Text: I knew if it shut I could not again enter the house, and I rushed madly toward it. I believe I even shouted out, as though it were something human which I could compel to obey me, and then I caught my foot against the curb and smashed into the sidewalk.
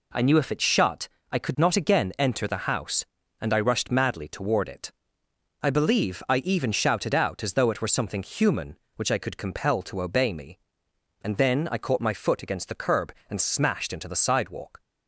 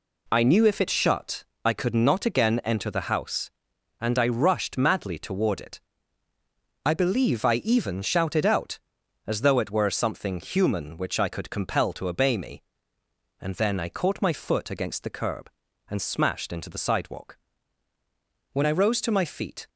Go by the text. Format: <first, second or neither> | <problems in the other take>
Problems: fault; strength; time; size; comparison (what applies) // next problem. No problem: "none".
first | pauses between "shut" and "I"; slight; at 1.4 s; 0.18 s long; slight in the first // goes on to say "When I rose to my feet"; noticeable; from 18.5 s on; 1.1 s long